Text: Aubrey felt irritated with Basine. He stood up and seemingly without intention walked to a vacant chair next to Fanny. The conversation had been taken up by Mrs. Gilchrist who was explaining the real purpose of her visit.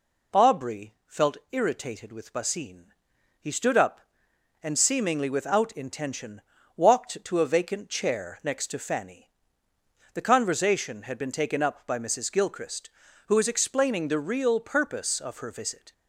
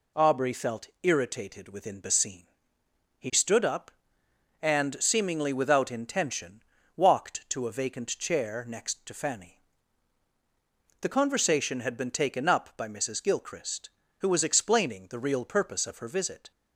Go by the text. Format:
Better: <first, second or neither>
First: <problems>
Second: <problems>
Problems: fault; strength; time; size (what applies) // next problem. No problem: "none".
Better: first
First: pauses between "intention" and "walked"; slight; at 6.4 s; 0.34 s long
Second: says "within" for "with"; at 1.6 s // pauses between "intention" and "walked"; slight; at 6.6 s; 0.32 s long